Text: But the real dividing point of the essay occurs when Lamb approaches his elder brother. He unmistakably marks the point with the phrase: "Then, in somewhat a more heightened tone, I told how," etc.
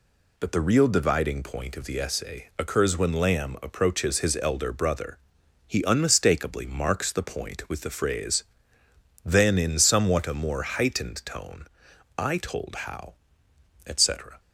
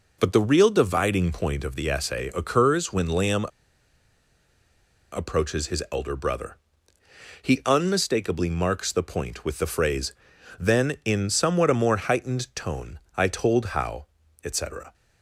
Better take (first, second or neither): first